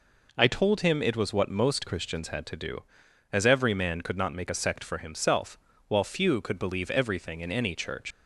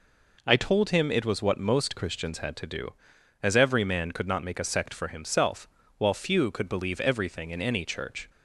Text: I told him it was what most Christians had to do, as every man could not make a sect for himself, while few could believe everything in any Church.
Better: second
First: leaves "Church" unfinished; at 8.1 s; 90 ms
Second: none

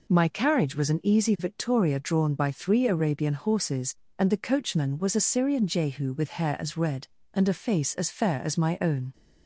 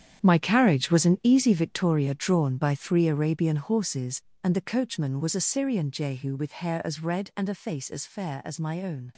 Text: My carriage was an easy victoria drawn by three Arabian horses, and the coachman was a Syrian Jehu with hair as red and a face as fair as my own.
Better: first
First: none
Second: gets quieter; strong; throughout; 12 dB

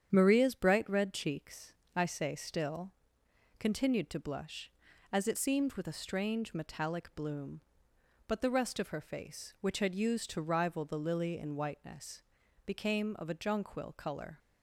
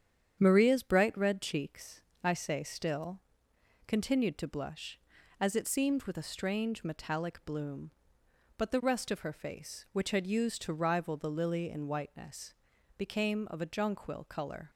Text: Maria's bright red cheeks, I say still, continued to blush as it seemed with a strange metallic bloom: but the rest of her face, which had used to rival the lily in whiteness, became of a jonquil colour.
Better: neither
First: starts louder than the rest; strong; until 1.1 s; 8.5 dB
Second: starts louder than the rest; strong; until 1.4 s; 8.5 dB

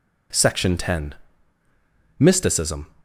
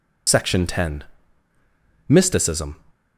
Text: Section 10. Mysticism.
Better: first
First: none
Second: loses the start of "Section"; at 0.2 s; 75 ms

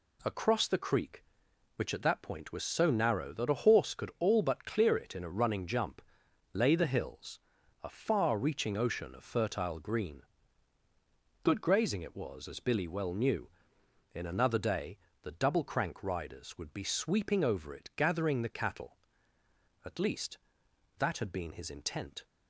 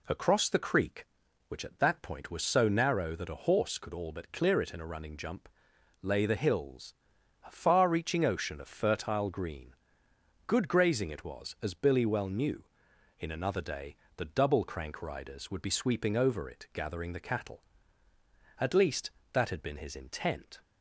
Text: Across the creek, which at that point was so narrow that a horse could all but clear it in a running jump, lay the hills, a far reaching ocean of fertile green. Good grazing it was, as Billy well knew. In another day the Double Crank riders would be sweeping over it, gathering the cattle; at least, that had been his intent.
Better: neither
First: pauses between "day" and "the"; slight; at 14.9 s; 0.24 s long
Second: pauses between "day" and "the"; slight; at 13.9 s; 0.20 s long

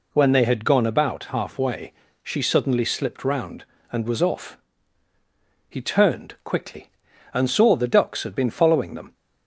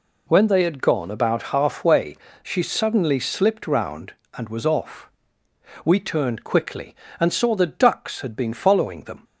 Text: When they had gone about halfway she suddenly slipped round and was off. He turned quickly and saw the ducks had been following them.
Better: first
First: pauses between "halfway" and "she"; slight; at 1.9 s; 0.28 s long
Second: pauses between "halfway" and "she"; slight; at 2.1 s; 0.30 s long // says "We" for "He"; at 5.8 s

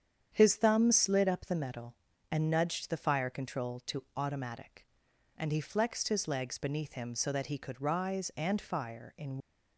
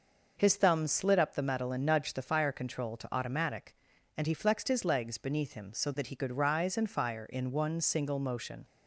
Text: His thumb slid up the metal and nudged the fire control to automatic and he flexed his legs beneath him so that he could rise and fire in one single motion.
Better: second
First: starts louder than the rest; strong; until 1.3 s; 8.5 dB // stops before "one single motion"; at 9.4 s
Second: none

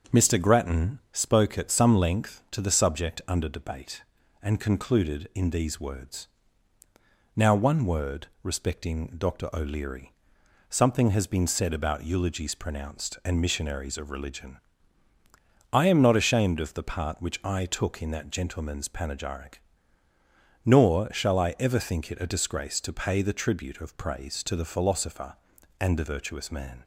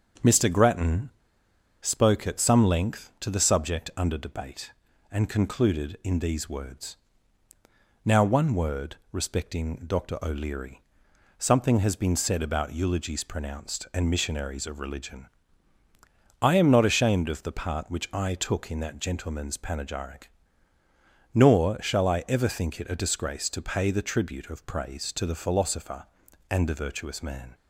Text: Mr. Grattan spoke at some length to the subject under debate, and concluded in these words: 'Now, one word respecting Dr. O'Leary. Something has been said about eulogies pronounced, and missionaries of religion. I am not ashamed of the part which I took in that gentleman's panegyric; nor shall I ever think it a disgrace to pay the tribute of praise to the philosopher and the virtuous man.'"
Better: first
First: starts louder than the rest; until 1.2 s; 7 dB // pauses between "word" and "respecting"; slight; at 8.2 s; 0.16 s long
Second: starts louder than the rest; until 1.9 s; 7 dB // pauses between "Grattan" and "spoke"; noticeable; at 1.1 s; 0.70 s long // pauses between "word" and "respecting"; slight; at 8.9 s; 0.16 s long

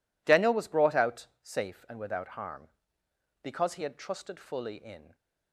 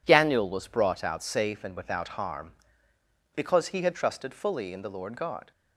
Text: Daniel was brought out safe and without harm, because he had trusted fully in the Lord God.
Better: second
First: pauses between "out" and "safe"; slight; at 1.2 s; 0.16 s long // stops before "the Lord God"; at 5.1 s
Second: none

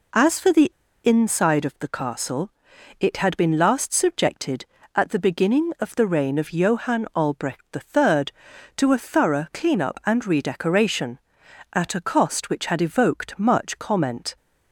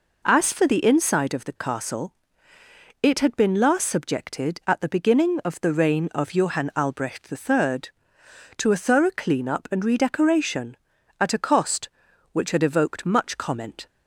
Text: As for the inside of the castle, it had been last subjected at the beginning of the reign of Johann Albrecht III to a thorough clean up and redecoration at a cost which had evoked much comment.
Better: second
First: pauses between "the" and "inside"; slight; at 0.7 s; 0.32 s long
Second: none

